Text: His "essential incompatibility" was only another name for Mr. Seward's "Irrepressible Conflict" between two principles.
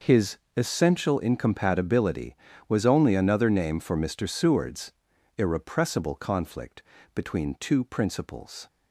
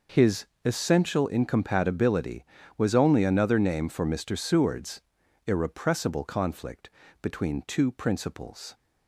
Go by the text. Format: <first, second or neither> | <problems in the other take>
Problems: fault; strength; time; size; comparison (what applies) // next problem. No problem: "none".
neither | pauses between "His" and "essential"; slight; the same in both // pauses between "Seward's" and "Irrepressible"; noticeable; the same in both // pauses between "Conflict" and "between"; slight; the same in both